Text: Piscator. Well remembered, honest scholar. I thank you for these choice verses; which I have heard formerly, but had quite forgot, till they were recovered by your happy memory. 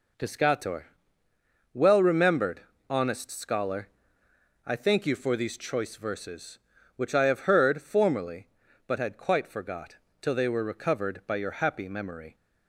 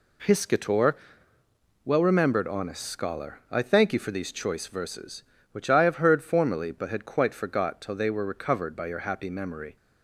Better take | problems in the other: neither | none

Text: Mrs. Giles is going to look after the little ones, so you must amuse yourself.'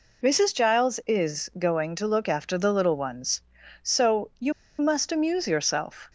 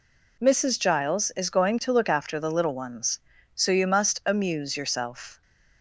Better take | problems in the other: second | pauses between "you" and "must"; slight; at 4.5 s; 0.27 s long

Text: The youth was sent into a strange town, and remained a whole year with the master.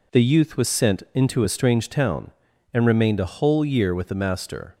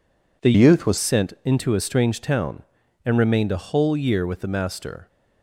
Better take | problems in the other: first | changes voice from "youth" to "was"; from 0.5 to 0.9 s; 0.4 s long

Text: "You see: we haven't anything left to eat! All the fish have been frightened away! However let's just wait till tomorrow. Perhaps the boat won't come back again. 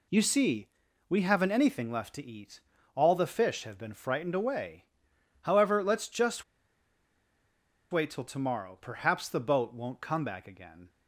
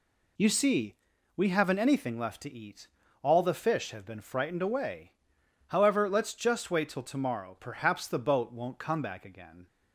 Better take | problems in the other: second | pauses between "just" and "wait"; strong; at 6.4 s; 1.4 s long

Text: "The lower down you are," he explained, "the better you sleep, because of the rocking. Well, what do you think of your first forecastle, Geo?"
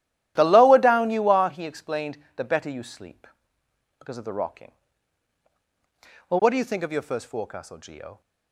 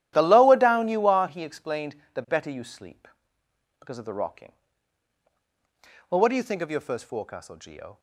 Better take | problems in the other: neither | starts louder than the rest; strong; the same in both

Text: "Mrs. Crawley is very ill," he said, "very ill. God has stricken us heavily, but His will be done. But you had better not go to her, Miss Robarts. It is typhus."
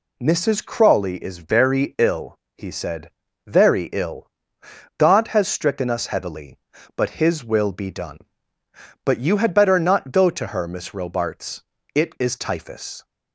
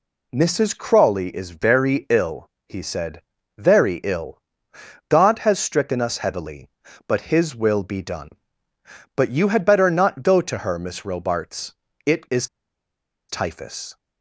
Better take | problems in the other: first | pauses between "is" and "typhus"; noticeable; at 12.4 s; 0.83 s long

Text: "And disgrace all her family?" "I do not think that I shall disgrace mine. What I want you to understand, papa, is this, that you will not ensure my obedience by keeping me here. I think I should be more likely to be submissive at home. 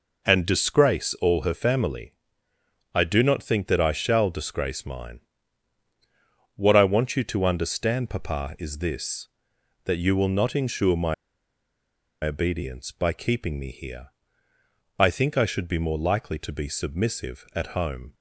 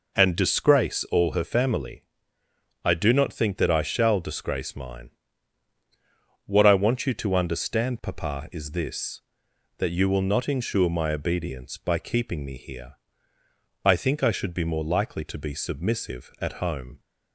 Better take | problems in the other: second | pauses between "my" and "obedience"; at 11.1 s; 1.0 s long

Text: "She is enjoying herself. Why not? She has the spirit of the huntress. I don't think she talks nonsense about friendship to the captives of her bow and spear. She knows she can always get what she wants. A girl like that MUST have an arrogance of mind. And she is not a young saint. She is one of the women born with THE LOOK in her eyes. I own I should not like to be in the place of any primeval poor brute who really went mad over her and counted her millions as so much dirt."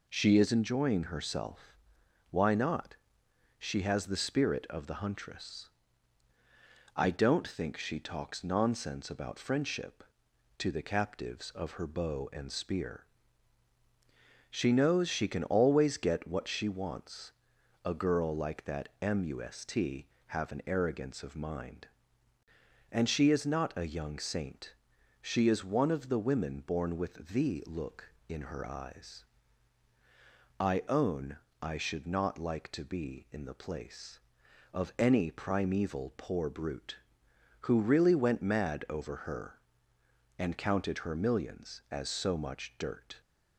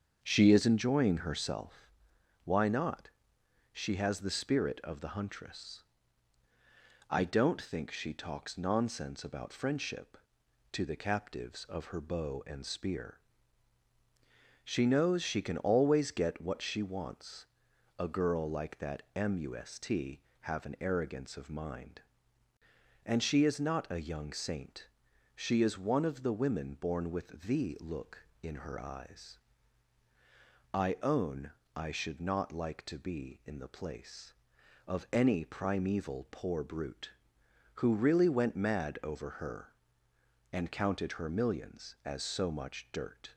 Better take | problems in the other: first | starts louder than the rest; until 1.6 s; 7 dB // pauses between "own" and "I"; slight; at 31.5 s; 0.24 s long; slight in the first

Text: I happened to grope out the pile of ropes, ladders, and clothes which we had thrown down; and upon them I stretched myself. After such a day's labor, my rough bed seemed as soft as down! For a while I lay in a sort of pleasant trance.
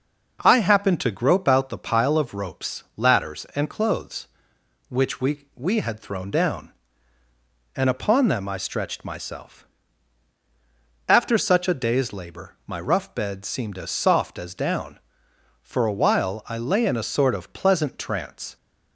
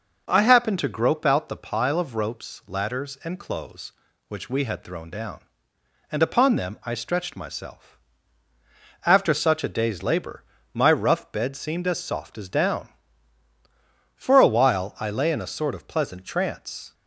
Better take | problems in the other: second | says "we" twice; at 5.5 s

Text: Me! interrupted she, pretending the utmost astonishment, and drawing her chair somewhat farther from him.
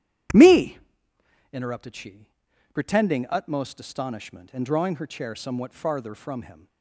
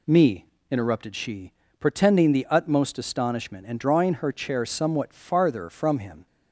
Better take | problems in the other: second | starts louder than the rest; strong; until 2.0 s; 11 dB // skips "the"; at 3.2 s

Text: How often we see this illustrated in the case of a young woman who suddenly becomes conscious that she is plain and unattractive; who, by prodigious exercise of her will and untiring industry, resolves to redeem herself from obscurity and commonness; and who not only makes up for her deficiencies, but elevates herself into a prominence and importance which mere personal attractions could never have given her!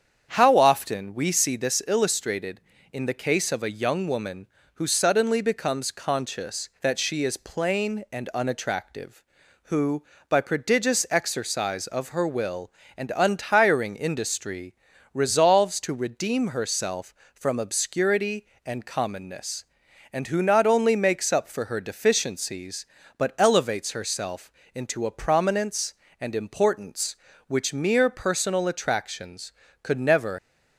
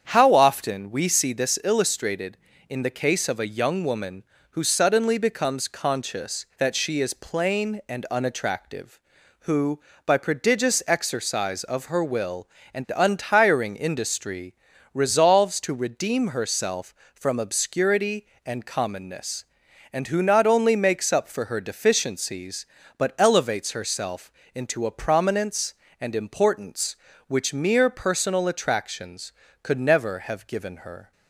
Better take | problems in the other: second | starts louder than the rest; strong; until 1.3 s; 8 dB; strong in the second // pauses between "herself" and "into"; slight; at 24.5 s; 0.24 s long; slight in the second // stops before "have given her"; at 30.3 s

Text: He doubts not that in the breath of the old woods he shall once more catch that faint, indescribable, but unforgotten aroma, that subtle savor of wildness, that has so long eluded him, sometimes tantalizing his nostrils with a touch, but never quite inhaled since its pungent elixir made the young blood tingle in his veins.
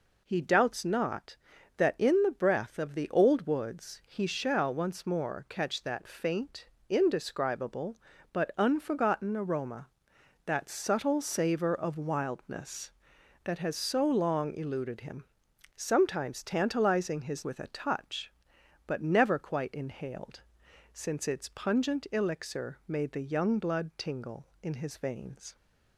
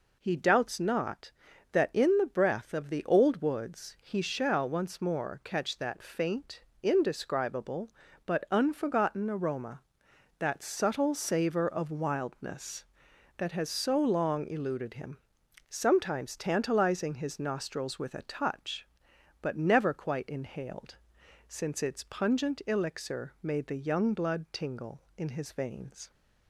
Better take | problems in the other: second | skips "nostrils"; at 17.4 s // pauses between "inhaled" and "since"; noticeable; at 20.4 s; 0.52 s long; noticeable in the second

